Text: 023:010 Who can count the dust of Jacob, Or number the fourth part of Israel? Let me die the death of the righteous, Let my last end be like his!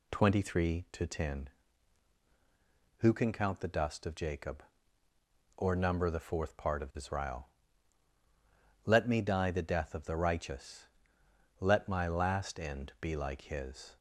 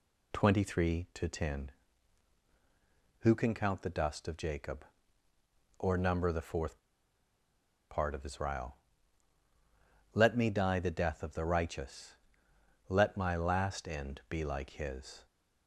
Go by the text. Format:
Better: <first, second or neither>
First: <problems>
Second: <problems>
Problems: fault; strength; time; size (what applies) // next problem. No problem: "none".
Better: first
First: none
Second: pauses between "fourth" and "part"; at 6.7 s; 1.1 s long